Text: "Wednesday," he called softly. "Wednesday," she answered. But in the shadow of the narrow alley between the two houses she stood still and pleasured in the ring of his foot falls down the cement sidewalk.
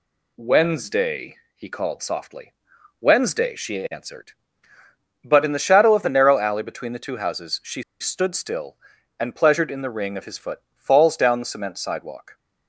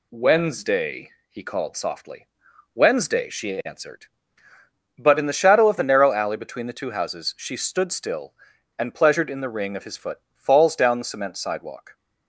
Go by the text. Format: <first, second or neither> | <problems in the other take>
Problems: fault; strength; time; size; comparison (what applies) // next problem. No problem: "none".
second | pauses between "she" and "stood"; slight; at 7.8 s; 0.18 s long